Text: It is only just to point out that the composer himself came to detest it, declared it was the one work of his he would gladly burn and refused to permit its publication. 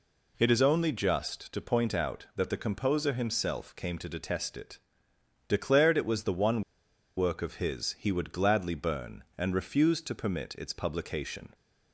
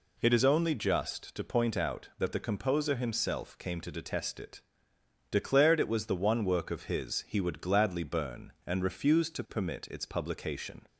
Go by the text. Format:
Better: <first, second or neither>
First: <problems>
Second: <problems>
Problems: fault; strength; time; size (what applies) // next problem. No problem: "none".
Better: second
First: pauses between "one" and "work"; noticeable; at 6.6 s; 0.56 s long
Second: none